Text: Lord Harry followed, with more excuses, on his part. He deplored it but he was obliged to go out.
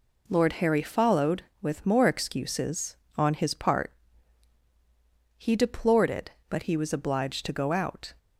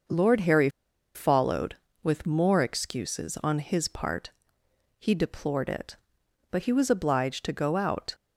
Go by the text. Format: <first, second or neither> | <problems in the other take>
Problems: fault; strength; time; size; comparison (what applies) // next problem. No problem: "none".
first | starts louder than the rest; noticeable; until 1.5 s; 6 dB // pauses between "Harry" and "followed"; noticeable; at 0.6 s; 0.46 s long